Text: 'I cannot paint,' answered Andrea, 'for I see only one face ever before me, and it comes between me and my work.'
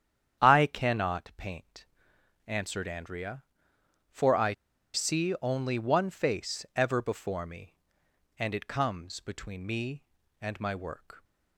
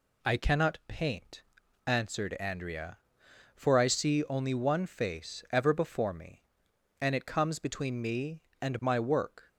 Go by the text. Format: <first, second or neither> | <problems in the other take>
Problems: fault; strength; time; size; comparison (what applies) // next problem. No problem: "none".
second | starts louder than the rest; strong; until 1.5 s; 9.5 dB // pauses between "I" and "see"; at 4.5 s; 0.41 s long